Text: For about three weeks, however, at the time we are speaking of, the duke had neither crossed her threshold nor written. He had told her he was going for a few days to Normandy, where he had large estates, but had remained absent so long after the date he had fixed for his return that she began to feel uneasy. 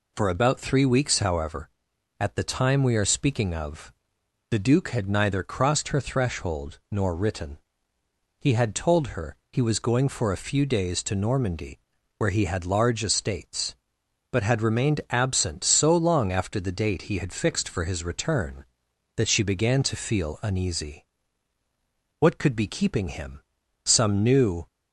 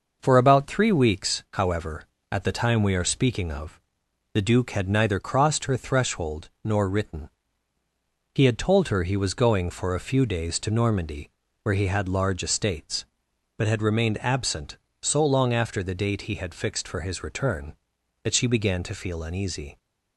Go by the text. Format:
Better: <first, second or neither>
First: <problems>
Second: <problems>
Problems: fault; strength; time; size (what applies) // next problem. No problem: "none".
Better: second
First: pauses between "her" and "he"; slight; at 9.3 s; 0.16 s long // goes on to say "What could be keeping him Some new"; strong; from 22.2 s on; 2.4 s long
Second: none